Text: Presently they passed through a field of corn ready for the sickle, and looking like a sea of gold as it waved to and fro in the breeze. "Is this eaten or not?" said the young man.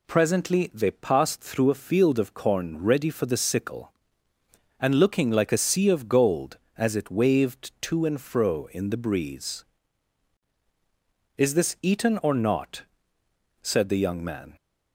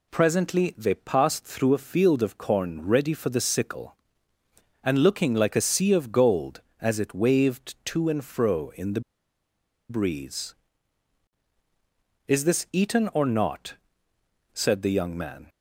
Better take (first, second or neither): first